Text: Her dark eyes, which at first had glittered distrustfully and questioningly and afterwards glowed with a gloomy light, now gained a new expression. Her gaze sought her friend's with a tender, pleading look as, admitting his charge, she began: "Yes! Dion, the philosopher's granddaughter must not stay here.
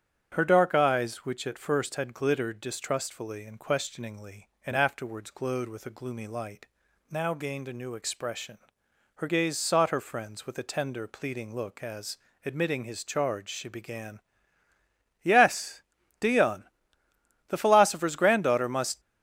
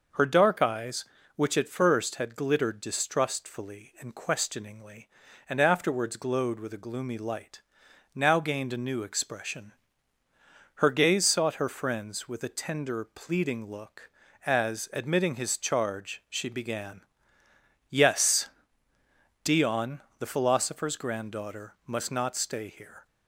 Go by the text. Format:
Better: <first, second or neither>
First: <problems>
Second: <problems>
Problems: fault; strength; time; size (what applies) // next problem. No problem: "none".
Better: second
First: starts louder than the rest; strong; until 1.3 s; 8.5 dB // stops before "not stay here"; at 18.9 s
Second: none